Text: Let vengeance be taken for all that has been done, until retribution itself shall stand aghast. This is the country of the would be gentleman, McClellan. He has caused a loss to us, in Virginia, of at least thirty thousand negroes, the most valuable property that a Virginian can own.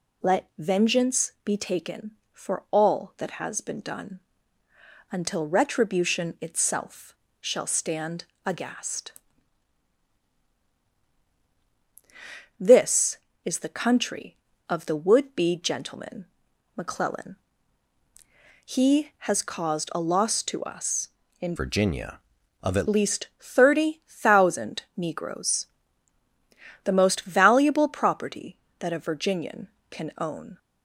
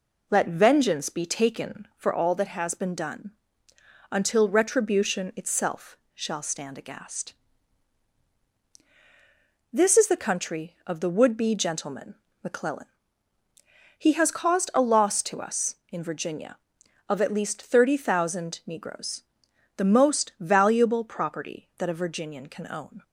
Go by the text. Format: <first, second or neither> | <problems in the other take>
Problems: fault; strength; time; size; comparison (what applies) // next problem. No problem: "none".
second | pauses between "itself" and "shall"; slight; at 7.1 s; 0.24 s long; slight in the second // pauses between "stand" and "aghast"; slight; at 8.2 s; 0.20 s long // changes voice from "Virginia" to "at"; from 21.5 to 22.8 s; 1.3 s long // pauses between "thousand" and "negroes"; slight; at 24.8 s; 0.16 s long